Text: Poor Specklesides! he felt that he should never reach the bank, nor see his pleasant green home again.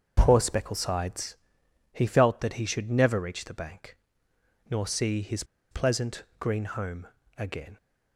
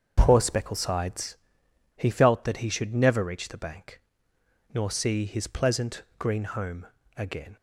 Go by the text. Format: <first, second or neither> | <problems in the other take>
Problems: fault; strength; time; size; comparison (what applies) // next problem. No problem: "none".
second | starts louder than the rest; until 1.1 s; 6.5 dB; also in the second // pauses between "his" and "pleasant"; slight; at 5.4 s; 0.26 s long // pauses between "home" and "again"; slight; at 7.0 s; 0.32 s long; slight in the second